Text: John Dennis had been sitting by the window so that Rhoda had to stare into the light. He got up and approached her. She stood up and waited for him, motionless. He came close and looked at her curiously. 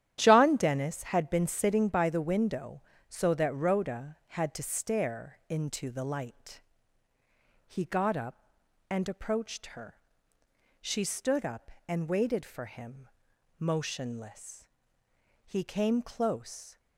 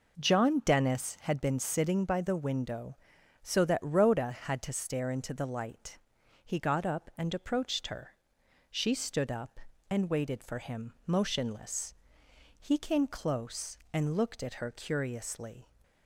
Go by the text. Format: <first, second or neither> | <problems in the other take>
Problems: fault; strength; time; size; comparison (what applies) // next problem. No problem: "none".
second | starts louder than the rest; strong; until 1.1 s; 11 dB // stops before "and looked at her curiously"; at 16.7 s